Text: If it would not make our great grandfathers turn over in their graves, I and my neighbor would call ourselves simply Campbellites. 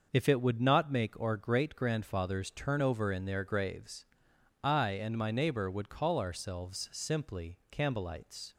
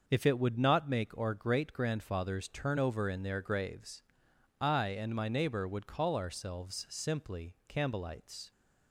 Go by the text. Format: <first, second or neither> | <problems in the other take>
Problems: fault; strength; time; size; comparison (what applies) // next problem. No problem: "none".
neither | starts louder than the rest; noticeable; the same in both // pauses between "simply" and "Campbellites"; slight; the same in both